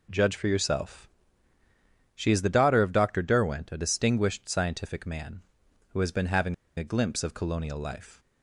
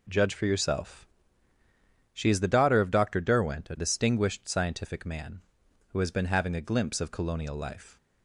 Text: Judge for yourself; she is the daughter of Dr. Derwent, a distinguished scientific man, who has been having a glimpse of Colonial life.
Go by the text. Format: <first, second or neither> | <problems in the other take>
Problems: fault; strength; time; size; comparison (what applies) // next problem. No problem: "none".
second | pauses between "having" and "a"; slight; at 6.5 s; 0.22 s long